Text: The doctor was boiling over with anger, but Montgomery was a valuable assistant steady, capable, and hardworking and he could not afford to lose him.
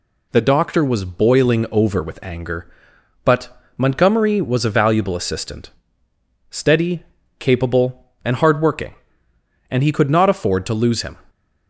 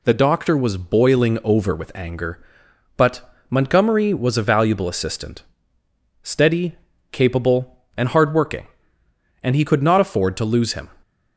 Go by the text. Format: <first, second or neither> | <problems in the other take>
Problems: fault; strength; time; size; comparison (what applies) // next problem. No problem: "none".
neither | pauses between "but" and "Montgomery"; slight; the same in both // pauses between "assistant" and "steady"; noticeable; the same in both